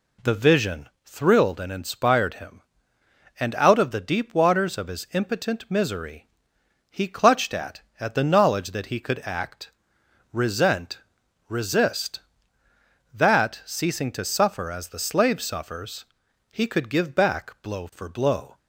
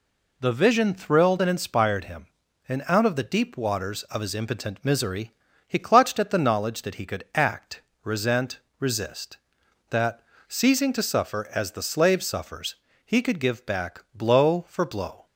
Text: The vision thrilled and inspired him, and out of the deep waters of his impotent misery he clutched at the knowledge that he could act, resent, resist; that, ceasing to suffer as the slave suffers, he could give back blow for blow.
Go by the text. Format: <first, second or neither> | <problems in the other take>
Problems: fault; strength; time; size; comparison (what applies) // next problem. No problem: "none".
second | pauses between "vision" and "thrilled"; slight; at 0.8 s; 0.16 s long // pauses between "misery" and "he"; noticeable; at 6.2 s; 0.64 s long; slight in the second // says "at" twice; at 8.0 s